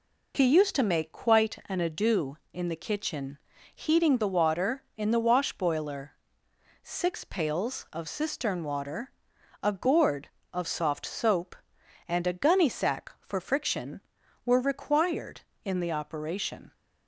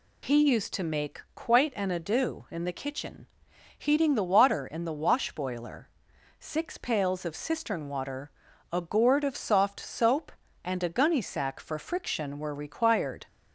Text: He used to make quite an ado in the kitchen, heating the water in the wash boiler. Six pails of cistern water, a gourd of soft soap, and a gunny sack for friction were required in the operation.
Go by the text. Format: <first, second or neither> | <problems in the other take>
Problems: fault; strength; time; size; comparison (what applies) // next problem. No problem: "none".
first | stops before "in the operation"; at 13.2 s